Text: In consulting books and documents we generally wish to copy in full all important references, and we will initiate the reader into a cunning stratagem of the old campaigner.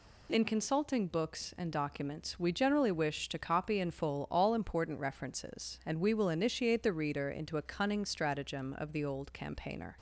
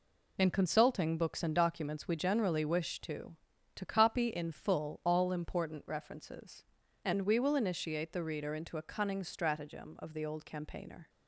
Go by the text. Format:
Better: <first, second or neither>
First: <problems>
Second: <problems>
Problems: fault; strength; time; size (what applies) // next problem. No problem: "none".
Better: first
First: none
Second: says "to" twice; at 3.7 s